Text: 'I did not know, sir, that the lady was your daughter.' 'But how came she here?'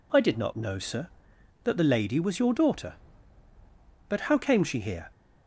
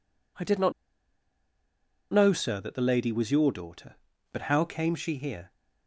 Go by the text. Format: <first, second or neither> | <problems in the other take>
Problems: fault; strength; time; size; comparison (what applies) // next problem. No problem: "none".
first | pauses between "not" and "know"; strong; at 0.7 s; 1.3 s long